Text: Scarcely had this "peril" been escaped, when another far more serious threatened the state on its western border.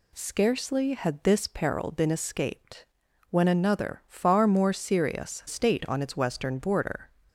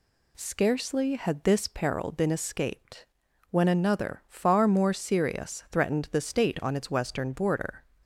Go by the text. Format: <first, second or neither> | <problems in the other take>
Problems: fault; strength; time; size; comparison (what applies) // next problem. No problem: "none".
second | skips "threatened the"; at 5.4 s